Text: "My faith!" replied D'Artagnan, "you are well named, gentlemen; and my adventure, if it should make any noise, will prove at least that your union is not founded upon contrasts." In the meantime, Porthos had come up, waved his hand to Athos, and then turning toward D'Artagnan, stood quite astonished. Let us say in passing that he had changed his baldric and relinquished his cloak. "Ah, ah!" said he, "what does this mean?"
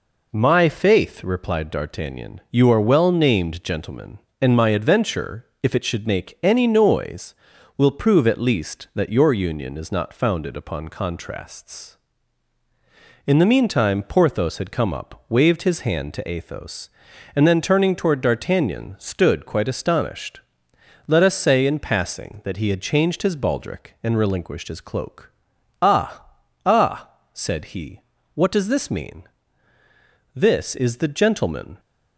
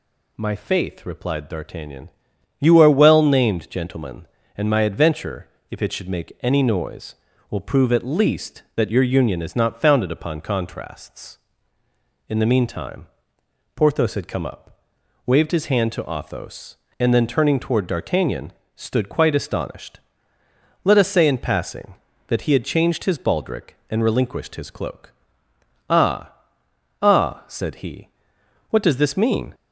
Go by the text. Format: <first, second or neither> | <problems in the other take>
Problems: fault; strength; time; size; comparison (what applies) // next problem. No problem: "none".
second | goes on to say "This is the gentleman"; from 30.3 s on; 1.4 s long